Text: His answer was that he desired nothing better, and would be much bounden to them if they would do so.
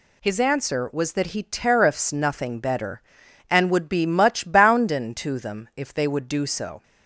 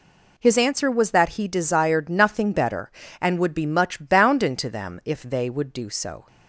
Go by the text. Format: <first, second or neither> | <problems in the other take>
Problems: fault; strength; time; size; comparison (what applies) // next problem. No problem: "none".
second | says "tariffs" for "desired"; at 1.4 s